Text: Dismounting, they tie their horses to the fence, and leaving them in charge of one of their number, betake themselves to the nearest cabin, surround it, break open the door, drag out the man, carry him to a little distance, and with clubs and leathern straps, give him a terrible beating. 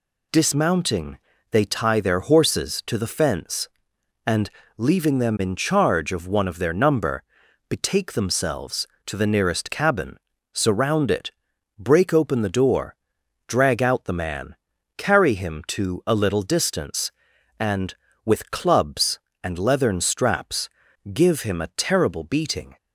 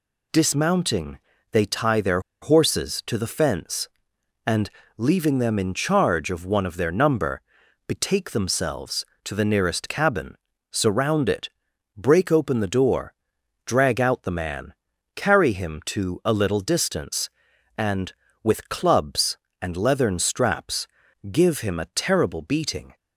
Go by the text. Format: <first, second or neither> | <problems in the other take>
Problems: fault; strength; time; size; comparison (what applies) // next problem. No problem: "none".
first | pauses between "their" and "horses"; slight; at 2.1 s; 0.22 s long // pauses between "and" and "leaving"; slight; at 4.7 s; 0.26 s long; slight in the first